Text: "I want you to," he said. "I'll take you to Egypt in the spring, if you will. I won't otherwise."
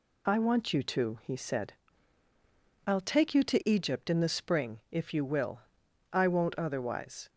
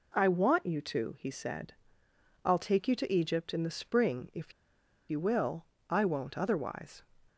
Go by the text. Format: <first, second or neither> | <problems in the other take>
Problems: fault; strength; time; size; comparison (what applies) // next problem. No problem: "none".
first | pauses between "if" and "you"; noticeable; at 4.5 s; 0.57 s long